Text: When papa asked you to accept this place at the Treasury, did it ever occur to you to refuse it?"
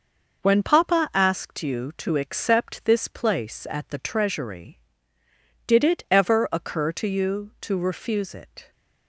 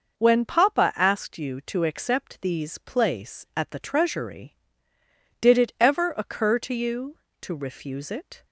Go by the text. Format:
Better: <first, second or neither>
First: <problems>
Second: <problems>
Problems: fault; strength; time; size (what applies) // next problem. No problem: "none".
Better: first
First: none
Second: says "these" for "this"; at 2.4 s